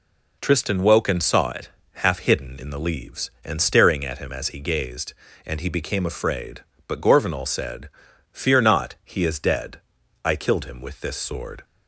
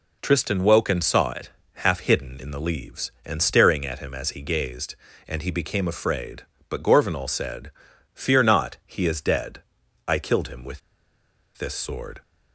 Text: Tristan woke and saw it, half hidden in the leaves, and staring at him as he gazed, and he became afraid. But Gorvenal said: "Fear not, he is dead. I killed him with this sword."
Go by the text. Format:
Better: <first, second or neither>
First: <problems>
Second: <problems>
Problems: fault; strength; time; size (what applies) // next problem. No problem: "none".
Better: first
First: none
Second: pauses between "with" and "this"; noticeable; at 10.8 s; 0.77 s long